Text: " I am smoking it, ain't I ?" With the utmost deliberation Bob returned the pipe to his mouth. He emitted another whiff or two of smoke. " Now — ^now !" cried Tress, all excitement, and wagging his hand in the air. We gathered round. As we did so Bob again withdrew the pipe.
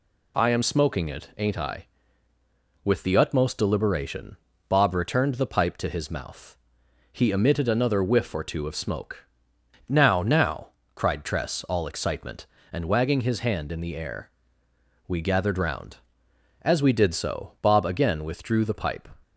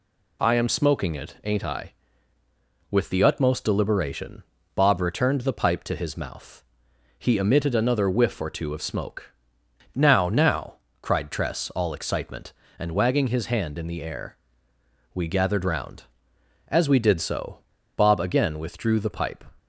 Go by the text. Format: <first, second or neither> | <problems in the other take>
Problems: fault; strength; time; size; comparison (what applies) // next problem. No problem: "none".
first | pauses between "deliberation" and "Bob"; slight; at 4.4 s; 0.32 s long; slight in the first // pauses between "so" and "Bob"; at 17.5 s; 0.39 s long